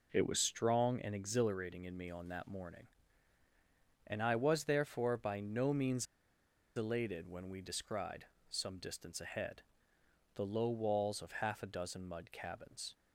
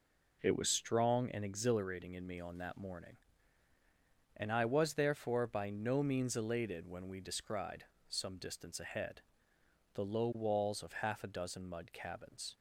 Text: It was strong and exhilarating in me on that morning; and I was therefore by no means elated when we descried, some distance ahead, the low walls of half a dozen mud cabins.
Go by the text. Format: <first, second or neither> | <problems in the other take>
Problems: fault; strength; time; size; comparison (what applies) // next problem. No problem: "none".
second | pauses between "means" and "elated"; noticeable; at 6.0 s; 0.71 s long